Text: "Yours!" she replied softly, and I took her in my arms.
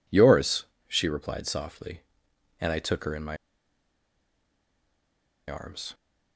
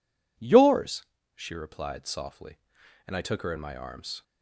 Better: second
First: pauses between "my" and "arms"; strong; at 3.3 s; 2.1 s long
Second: none

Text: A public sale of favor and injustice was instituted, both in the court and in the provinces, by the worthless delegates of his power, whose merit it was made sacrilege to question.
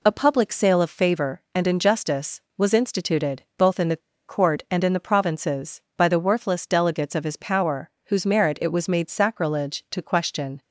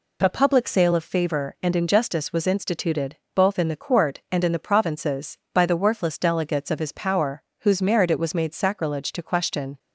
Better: second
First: pauses between "the" and "court"; slight; at 4.0 s; 0.28 s long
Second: none

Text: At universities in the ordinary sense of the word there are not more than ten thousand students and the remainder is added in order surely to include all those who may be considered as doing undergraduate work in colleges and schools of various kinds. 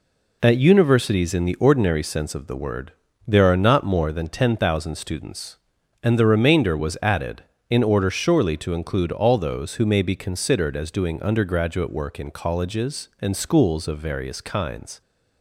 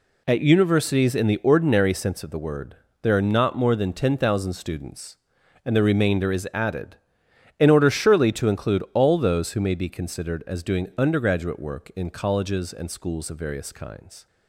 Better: second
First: pauses between "word" and "there"; slight; at 2.9 s; 0.34 s long // says "was" for "is"; at 6.7 s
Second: pauses between "word" and "there"; slight; at 2.7 s; 0.24 s long

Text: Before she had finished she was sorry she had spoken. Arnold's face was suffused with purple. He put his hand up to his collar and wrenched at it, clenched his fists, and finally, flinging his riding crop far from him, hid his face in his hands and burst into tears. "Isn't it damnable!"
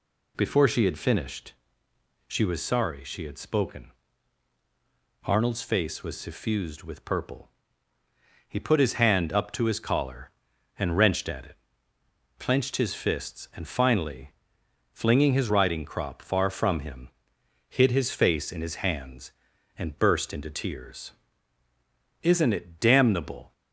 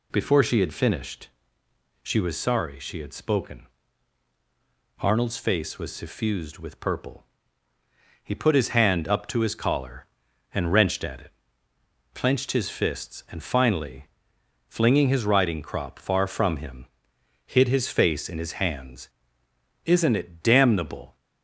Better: first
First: pauses between "finished" and "she"; noticeable; at 1.5 s; 0.74 s long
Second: pauses between "finished" and "she"; noticeable; at 1.2 s; 0.74 s long // skips "and burst into tears"; at 19.4 s

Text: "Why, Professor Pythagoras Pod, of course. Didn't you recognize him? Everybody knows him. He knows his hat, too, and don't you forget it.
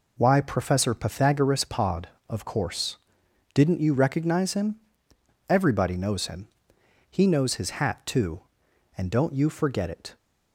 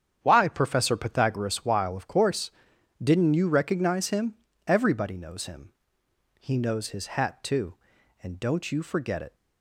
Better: first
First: none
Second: starts louder than the rest; strong; until 1.2 s; 8.5 dB // says "Weil" for "Pod"; at 1.6 s

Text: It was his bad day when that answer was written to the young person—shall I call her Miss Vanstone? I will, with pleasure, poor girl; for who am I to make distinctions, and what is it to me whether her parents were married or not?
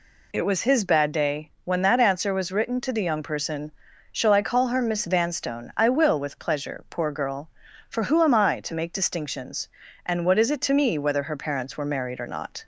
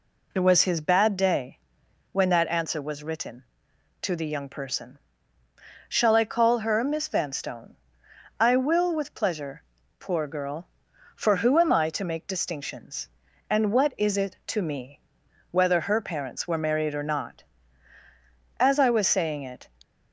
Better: first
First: none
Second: pauses between "day" and "when"; noticeable; at 1.5 s; 0.54 s long // pauses between "me" and "whether"; noticeable; at 15.0 s; 0.50 s long // goes on to say "As I was saying it"; noticeable; from 18.6 s on; 1.0 s long

